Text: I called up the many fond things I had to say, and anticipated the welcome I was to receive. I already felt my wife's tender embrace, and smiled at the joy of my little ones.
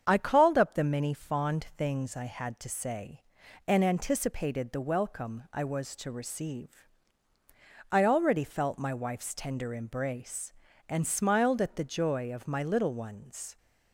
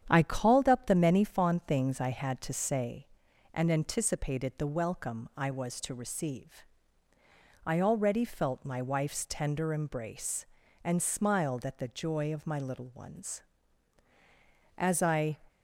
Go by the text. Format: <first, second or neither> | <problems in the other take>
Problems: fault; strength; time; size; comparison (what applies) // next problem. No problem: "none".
first | starts louder than the rest; strong; until 1.0 s; 9 dB; strong in the first // goes on to say "As I"; from 14.7 s on; 0.60 s long